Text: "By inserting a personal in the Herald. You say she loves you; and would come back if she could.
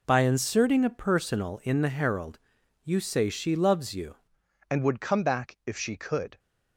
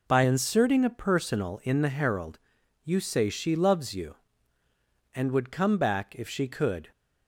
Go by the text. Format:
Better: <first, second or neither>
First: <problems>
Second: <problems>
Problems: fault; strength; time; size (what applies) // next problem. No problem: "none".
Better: second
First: changes voice at "and"; from 4.7 s on; 1.6 s long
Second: none